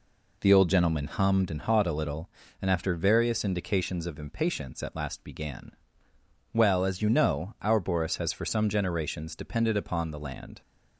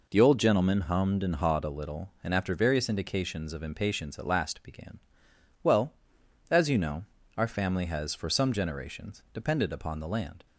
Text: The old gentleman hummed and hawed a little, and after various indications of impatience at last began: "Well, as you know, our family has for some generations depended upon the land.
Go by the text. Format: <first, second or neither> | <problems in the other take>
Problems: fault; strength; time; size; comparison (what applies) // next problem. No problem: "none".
second | says "boris" for "family"; at 7.8 s